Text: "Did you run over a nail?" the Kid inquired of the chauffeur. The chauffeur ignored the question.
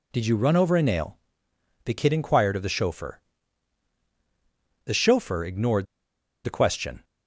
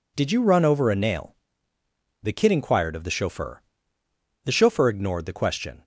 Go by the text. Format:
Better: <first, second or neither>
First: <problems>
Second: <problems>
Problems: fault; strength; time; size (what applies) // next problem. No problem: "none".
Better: second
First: pauses between "ignored" and "the"; noticeable; at 5.8 s; 0.59 s long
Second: none